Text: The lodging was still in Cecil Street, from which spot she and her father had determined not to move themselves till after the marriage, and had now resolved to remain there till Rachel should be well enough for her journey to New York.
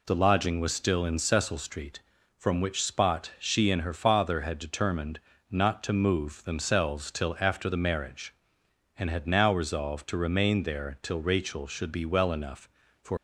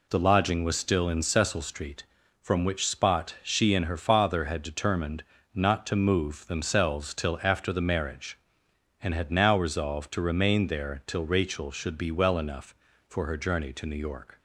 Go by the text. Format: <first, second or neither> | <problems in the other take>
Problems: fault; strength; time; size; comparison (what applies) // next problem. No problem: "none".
second | pauses between "determined" and "not"; slight; at 5.1 s; 0.28 s long; slight in the second // stops before "her journey to New York"; at 13.1 s